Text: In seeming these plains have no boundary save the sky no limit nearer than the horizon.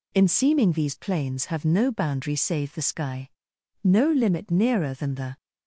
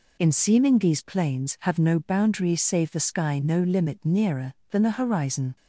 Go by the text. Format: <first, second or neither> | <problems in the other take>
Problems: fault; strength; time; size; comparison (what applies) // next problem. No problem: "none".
second | pauses between "sky" and "no"; noticeable; at 3.3 s; 0.54 s long // stops before "horizon"; at 5.3 s